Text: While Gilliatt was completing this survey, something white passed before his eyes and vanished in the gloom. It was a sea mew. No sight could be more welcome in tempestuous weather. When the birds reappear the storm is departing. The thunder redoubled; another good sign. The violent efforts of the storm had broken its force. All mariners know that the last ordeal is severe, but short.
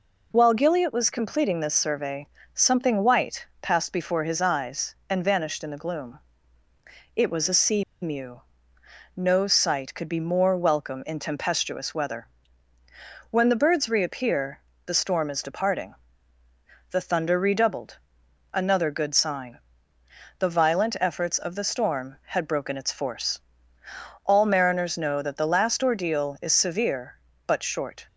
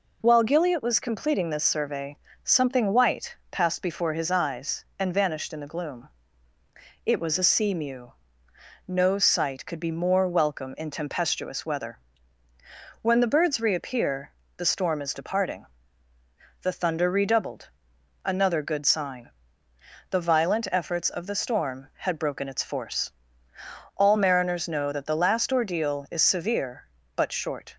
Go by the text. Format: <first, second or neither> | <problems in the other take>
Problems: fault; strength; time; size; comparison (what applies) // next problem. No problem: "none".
second | pauses between "white" and "passed"; slight; at 3.4 s; 0.16 s long; slight in the second // pauses between "sea" and "mew"; slight; at 7.8 s; 0.19 s long // pauses between "reappear" and "the"; slight; at 14.5 s; 0.28 s long; slight in the second